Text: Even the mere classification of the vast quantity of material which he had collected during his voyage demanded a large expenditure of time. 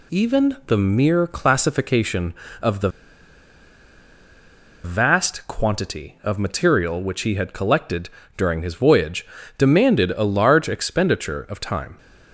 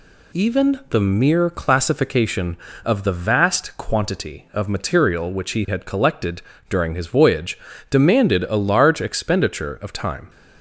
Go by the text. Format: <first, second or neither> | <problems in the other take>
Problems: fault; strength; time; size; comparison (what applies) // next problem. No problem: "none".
second | pauses between "the" and "vast"; strong; at 2.9 s; 1.9 s long // pauses between "collected" and "during"; slight; at 8.0 s; 0.26 s long; slight in the second // pauses between "voyage" and "demanded"; slight; at 9.2 s; 0.32 s long; slight in the second